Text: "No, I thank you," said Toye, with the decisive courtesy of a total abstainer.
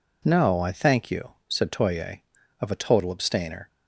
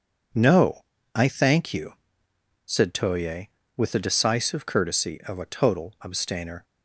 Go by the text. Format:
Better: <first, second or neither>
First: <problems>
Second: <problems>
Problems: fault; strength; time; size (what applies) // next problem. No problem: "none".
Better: second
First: skips "with the decisive courtesy"; at 2.4 s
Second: none